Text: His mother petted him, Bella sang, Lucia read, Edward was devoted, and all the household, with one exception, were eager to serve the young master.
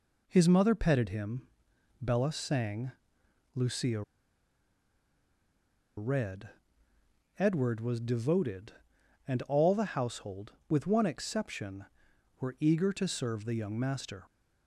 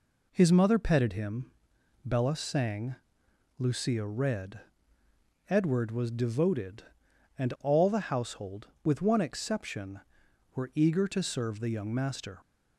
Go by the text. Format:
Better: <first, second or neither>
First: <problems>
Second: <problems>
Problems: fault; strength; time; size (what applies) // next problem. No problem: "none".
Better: second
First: pauses between "Lucia" and "read"; strong; at 4.0 s; 1.9 s long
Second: none